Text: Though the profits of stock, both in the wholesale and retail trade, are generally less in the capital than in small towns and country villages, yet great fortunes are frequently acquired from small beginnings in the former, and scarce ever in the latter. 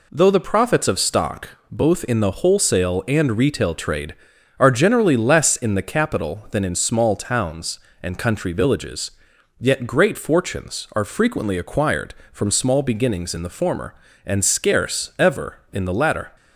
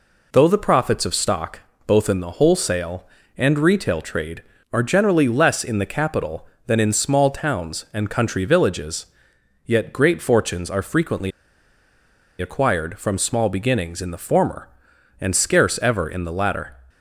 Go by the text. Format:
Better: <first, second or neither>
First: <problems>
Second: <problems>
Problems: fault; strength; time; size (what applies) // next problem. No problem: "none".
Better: first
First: none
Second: pauses between "frequently" and "acquired"; at 11.3 s; 1.0 s long